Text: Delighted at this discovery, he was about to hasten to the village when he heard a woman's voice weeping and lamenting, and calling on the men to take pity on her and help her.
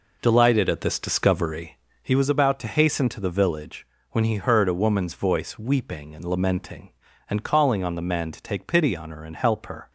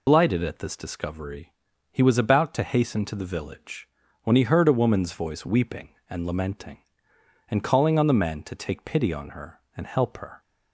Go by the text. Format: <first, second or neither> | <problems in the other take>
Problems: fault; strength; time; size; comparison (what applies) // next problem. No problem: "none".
first | loses the start of "Delighted"; at 0.0 s; 100 ms // pauses between "village" and "when"; at 3.8 s; 0.38 s long; slight in the first